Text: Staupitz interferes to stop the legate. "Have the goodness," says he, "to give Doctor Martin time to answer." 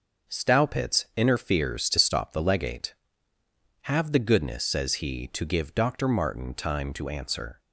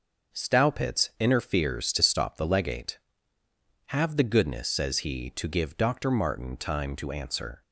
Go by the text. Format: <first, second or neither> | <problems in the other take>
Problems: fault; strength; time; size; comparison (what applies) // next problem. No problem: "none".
neither | none